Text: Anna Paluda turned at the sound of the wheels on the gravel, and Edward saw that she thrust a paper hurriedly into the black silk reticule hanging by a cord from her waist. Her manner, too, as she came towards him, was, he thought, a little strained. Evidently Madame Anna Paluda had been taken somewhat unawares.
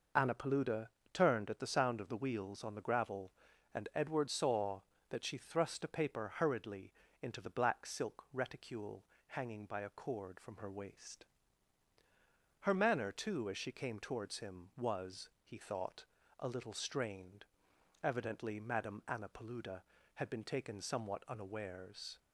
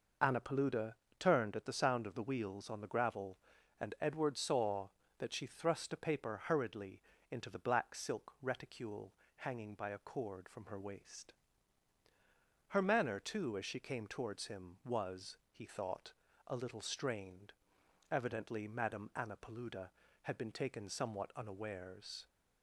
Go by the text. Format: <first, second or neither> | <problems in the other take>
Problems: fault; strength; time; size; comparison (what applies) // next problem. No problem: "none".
neither | pauses between "Paluda" and "turned"; slight; the same in both // pauses between "hurriedly" and "into"; slight; the same in both // pauses between "reticule" and "hanging"; slight; the same in both